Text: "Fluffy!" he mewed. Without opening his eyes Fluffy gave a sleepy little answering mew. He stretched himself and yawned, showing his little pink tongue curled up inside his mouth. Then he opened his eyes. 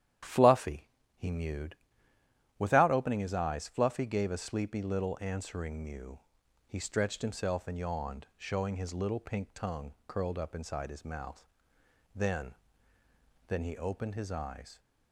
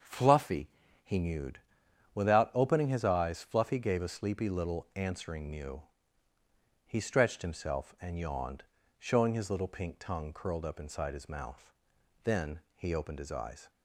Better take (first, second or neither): second